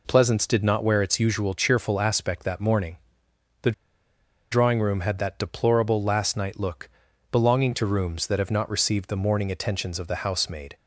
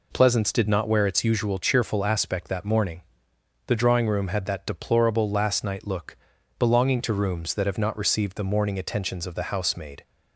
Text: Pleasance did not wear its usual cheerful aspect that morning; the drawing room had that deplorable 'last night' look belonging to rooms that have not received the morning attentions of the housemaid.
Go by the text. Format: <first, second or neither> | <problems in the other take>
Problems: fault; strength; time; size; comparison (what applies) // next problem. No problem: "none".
second | pauses between "the" and "drawing"; noticeable; at 3.7 s; 0.79 s long // pauses between "look" and "belonging"; at 6.8 s; 0.42 s long; also in the second